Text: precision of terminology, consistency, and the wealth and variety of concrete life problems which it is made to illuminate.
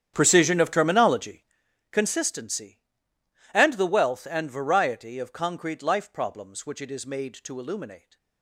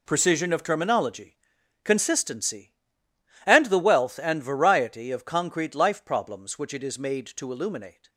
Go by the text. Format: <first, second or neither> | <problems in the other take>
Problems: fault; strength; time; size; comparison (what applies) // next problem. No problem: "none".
second | starts louder than the rest; strong; until 1.6 s; 9.5 dB